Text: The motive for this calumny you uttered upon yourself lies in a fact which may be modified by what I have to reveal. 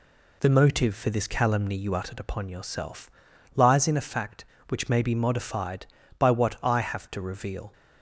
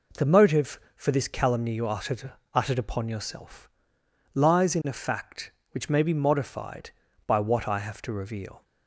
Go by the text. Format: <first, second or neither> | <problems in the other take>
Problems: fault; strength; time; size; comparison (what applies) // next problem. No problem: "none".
first | says "uttered" twice; at 2.5 s // pauses between "yourself" and "lies"; noticeable; at 3.6 s; 0.64 s long; also in the first